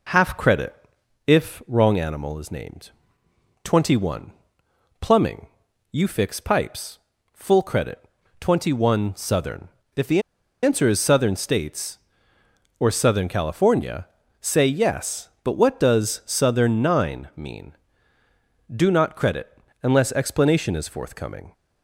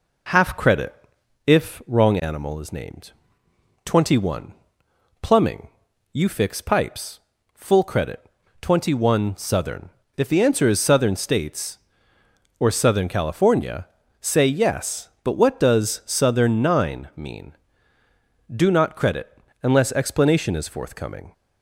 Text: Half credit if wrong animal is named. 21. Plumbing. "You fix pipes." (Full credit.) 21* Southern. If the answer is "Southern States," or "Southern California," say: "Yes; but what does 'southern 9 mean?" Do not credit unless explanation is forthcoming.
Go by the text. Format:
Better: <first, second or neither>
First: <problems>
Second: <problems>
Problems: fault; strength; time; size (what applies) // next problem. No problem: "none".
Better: second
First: pauses between "credit" and "if"; noticeable; at 0.7 s; 0.52 s long // pauses between "the" and "answer"; at 10.2 s; 0.41 s long // pauses between "credit" and "unless"; slight; at 19.5 s; 0.28 s long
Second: pauses between "credit" and "if"; noticeable; at 0.9 s; 0.52 s long // pauses between "credit" and "unless"; slight; at 19.3 s; 0.28 s long